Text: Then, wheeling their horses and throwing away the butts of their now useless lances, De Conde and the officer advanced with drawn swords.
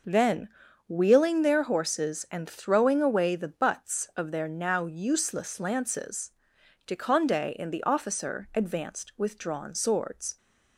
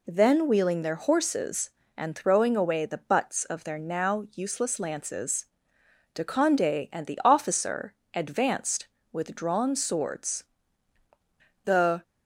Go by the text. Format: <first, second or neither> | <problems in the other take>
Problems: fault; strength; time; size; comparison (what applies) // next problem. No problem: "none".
first | pauses between "officer" and "advanced"; slight; at 7.9 s; 0.18 s long // goes on to say "The"; slight; from 11.6 s on; 0.38 s long